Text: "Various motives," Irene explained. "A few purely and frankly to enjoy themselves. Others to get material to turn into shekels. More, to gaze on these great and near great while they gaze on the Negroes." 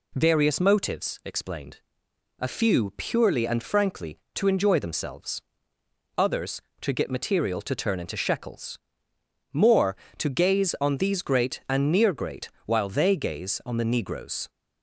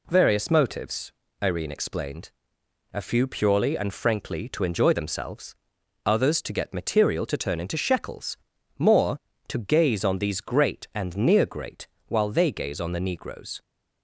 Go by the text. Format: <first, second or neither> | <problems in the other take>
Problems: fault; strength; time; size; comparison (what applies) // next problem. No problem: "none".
second | skips "Irene"; at 1.2 s // pauses between "great" and "while"; slight; at 12.4 s; 0.16 s long; slight in the second